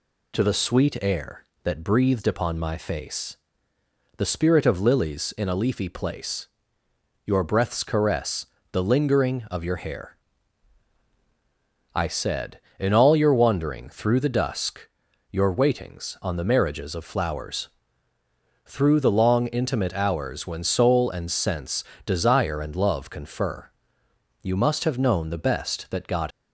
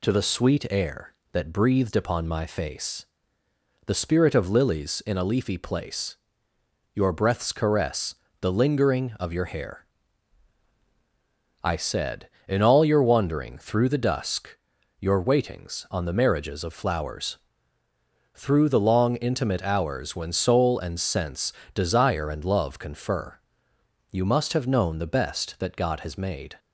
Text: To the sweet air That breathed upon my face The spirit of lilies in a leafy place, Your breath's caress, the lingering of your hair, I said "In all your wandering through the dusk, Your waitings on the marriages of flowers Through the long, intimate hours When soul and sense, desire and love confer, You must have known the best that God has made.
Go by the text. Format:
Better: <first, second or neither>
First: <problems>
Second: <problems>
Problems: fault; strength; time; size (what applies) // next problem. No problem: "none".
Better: second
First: pauses between "face" and "The"; noticeable; at 3.3 s; 0.82 s long // pauses between "flowers" and "Through"; noticeable; at 17.6 s; 0.96 s long // stops before "has made"; at 26.3 s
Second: pauses between "face" and "The"; noticeable; at 3.0 s; 0.82 s long // pauses between "flowers" and "Through"; noticeable; at 17.3 s; 0.96 s long